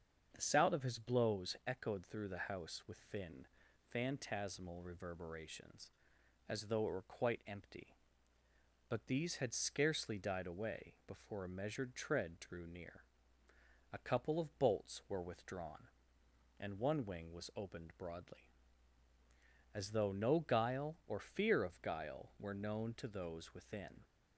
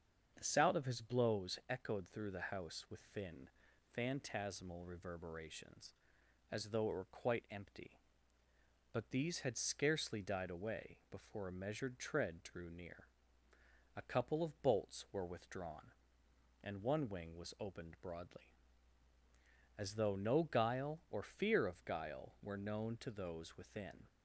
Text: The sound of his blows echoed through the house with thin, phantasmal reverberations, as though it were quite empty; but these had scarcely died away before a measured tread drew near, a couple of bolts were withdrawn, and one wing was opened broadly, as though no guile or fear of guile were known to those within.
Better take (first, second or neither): neither